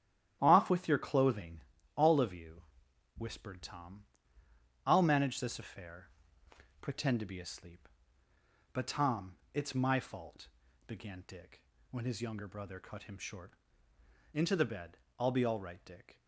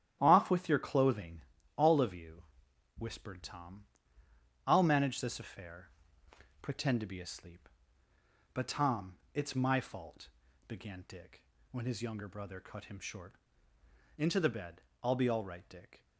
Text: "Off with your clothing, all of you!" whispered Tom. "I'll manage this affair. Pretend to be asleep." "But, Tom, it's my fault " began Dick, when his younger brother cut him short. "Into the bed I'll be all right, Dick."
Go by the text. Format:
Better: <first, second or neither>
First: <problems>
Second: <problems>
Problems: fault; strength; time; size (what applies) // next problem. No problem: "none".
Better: neither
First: starts louder than the rest; strong; until 1.4 s; 11 dB // pauses between "bed" and "I'll"; slight; at 14.9 s; 0.20 s long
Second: starts louder than the rest; strong; until 1.2 s; 11 dB // pauses between "bed" and "I'll"; slight; at 14.8 s; 0.20 s long